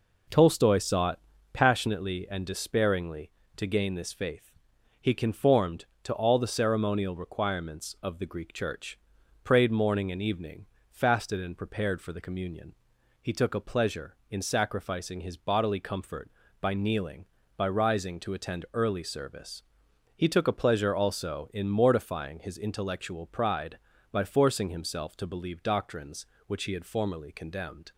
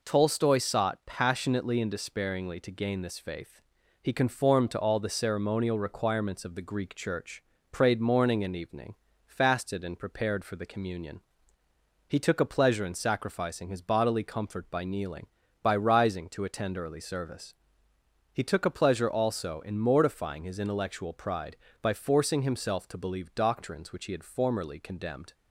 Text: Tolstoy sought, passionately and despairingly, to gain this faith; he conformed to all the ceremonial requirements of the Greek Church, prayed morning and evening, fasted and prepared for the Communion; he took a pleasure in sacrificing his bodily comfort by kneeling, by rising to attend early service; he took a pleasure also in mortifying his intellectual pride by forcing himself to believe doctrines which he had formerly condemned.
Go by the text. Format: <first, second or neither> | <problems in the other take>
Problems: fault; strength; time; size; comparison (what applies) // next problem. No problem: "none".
neither | none